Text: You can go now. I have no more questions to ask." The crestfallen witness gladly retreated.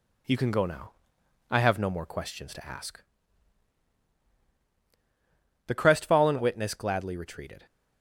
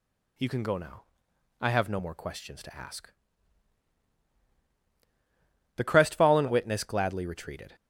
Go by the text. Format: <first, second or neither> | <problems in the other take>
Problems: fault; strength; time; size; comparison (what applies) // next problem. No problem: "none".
second | gets quieter; slight; throughout; 2.5 dB